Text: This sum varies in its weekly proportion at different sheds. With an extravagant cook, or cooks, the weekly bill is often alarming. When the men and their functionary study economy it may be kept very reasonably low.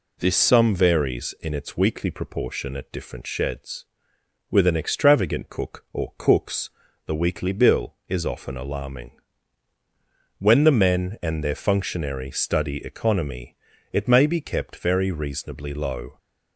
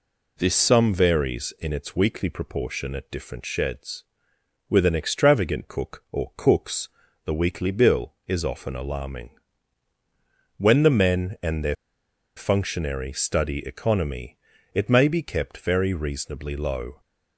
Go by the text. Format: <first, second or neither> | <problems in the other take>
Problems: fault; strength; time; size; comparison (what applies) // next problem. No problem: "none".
first | pauses between "their" and "functionary"; noticeable; at 11.7 s; 0.61 s long // pauses between "economy" and "it"; slight; at 14.3 s; 0.36 s long; slight in the first